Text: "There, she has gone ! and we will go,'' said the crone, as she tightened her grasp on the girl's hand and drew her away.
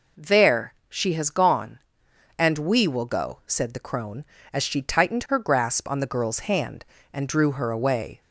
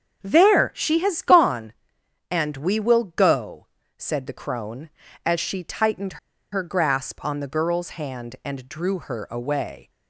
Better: first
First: none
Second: starts louder than the rest; until 1.2 s; 7 dB // pauses between "tightened" and "her"; slight; at 6.1 s; 0.34 s long

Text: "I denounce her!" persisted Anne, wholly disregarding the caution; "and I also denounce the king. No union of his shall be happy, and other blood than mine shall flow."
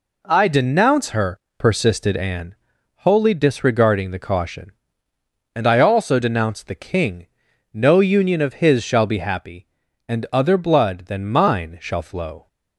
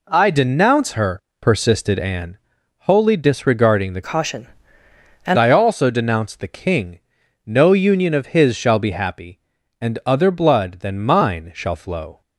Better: first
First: none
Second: changes voice from "caution" to "and"; from 4.0 to 5.3 s; 1.3 s long

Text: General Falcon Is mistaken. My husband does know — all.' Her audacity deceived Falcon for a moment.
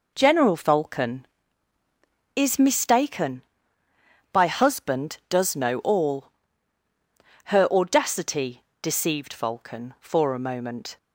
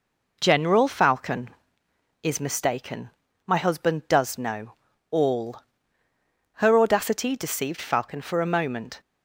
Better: second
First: says "By" for "My"; at 4.3 s // pauses between "audacity" and "deceived"; slight; at 8.6 s; 0.18 s long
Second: none

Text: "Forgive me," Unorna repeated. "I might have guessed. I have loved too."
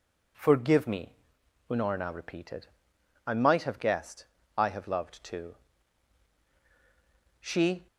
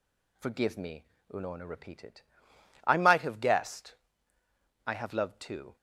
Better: second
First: goes on to say "She"; slight; from 7.3 s on; 0.48 s long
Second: none

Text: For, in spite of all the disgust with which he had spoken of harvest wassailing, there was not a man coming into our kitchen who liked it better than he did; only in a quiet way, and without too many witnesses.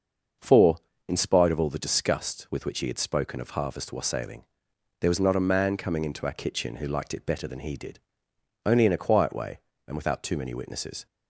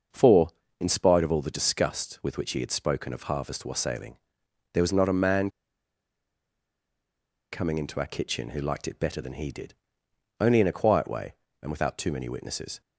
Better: first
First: starts louder than the rest; until 1.7 s; 6.5 dB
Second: starts louder than the rest; until 1.4 s; 6.5 dB // pauses between "man" and "coming"; strong; at 5.4 s; 2.0 s long

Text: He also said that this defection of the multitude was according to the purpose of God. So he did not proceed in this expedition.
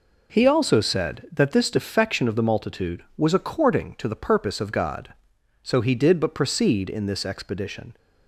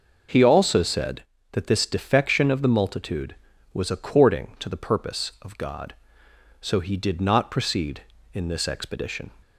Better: second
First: says "but" for "not"; at 6.2 s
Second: none

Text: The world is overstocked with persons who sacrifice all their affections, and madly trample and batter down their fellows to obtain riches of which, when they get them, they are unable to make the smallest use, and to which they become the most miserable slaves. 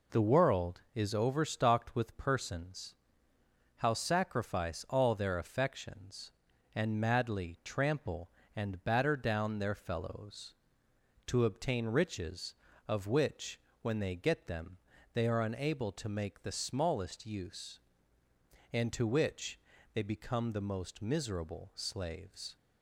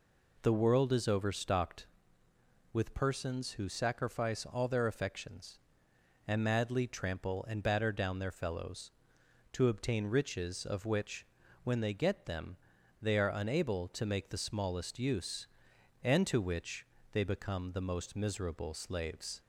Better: second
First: says "how" for "who"; at 3.7 s // pauses between "which" and "they"; slight; at 19.5 s; 0.36 s long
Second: pauses between "which" and "they"; slight; at 16.8 s; 0.26 s long

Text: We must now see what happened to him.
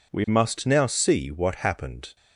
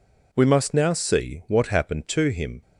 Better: second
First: stops before "to him"; at 2.1 s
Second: none

